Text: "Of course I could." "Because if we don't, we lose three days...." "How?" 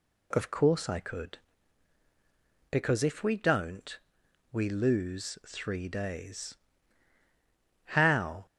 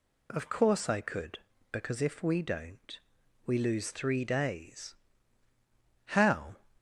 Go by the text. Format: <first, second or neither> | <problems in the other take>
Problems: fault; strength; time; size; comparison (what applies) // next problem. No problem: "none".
neither | none